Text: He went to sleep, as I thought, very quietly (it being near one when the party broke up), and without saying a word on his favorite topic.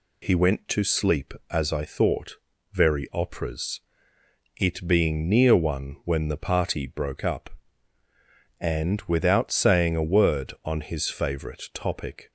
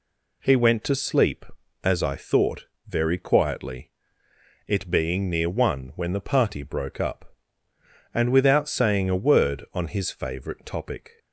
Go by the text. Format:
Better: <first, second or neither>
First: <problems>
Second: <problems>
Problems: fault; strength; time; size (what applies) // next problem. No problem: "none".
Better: second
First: says "operas" for "quietly"; at 3.1 s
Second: none